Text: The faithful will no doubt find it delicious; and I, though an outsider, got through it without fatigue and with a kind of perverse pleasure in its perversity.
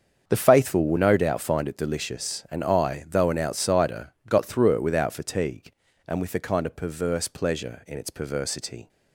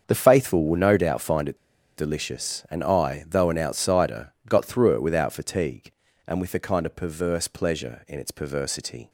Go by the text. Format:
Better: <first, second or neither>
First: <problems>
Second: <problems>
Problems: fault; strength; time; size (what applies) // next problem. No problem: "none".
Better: first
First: starts louder than the rest; until 1.2 s; 7 dB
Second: starts louder than the rest; until 1.0 s; 7 dB // pauses between "it" and "delicious"; at 1.5 s; 0.40 s long